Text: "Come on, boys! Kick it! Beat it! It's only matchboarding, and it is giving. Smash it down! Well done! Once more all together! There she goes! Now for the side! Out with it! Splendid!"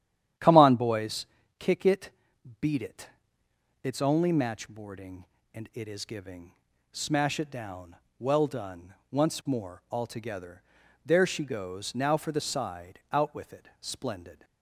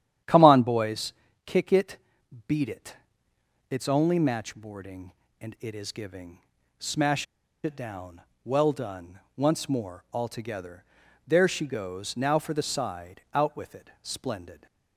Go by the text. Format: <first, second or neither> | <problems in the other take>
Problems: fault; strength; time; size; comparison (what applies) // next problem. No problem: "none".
first | starts louder than the rest; strong; until 1.5 s; 10.5 dB; strong in the first // pauses between "Smash" and "it"; at 7.2 s; 0.38 s long